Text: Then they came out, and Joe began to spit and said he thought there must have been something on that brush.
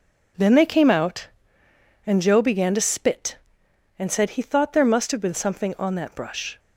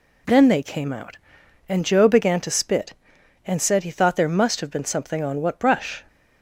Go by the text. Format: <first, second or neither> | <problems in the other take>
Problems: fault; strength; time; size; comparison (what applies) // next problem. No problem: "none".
first | says "what" for "that"; at 5.3 s